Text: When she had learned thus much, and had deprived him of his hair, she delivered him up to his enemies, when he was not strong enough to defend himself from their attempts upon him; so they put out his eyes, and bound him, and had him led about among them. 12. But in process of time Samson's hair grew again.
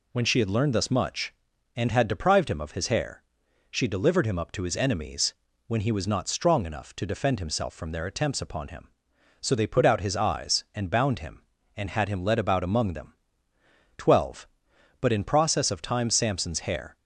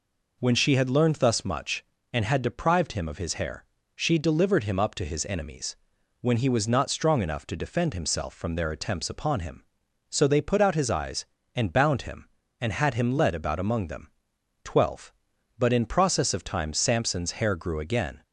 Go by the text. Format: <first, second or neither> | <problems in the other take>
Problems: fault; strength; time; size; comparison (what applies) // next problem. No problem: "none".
second | stops before "grew again"; at 16.9 s